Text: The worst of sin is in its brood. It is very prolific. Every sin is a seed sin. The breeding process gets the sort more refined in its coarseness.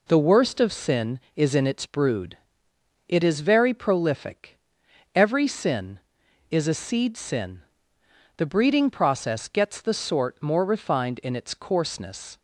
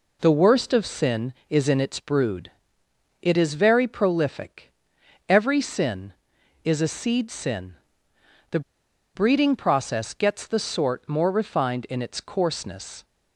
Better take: first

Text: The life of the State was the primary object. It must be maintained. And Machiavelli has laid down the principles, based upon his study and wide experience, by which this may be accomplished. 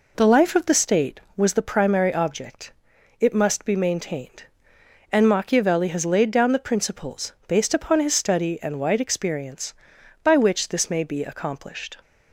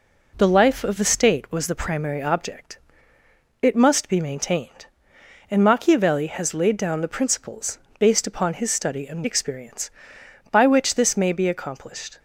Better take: first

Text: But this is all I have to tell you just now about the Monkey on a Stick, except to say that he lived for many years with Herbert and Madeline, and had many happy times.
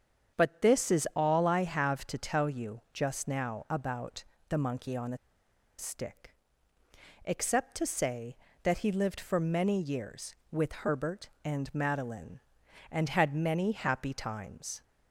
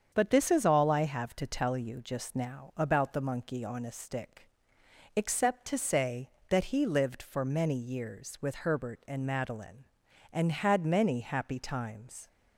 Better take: second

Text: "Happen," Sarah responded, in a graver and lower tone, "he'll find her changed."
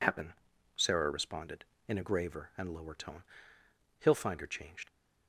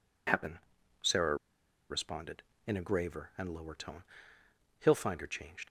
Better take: first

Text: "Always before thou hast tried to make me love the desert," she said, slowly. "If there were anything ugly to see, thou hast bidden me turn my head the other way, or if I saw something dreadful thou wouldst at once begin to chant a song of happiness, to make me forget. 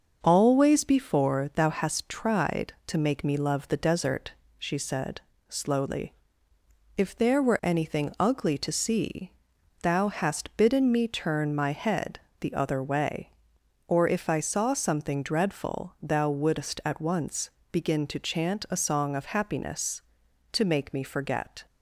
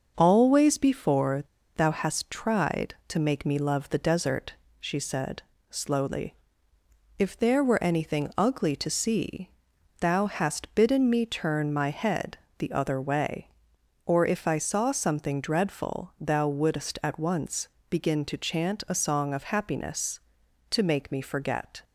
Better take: first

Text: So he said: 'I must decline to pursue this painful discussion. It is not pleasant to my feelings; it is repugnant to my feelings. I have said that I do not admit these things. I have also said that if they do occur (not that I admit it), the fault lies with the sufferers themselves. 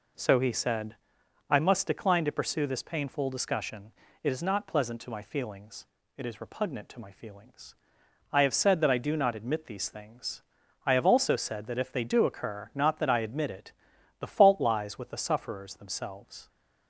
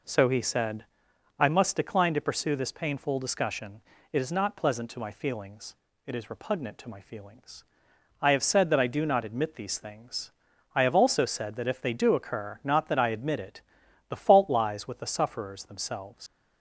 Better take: first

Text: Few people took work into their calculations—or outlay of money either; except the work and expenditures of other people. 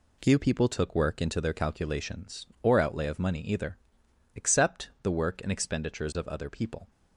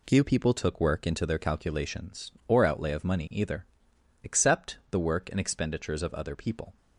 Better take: neither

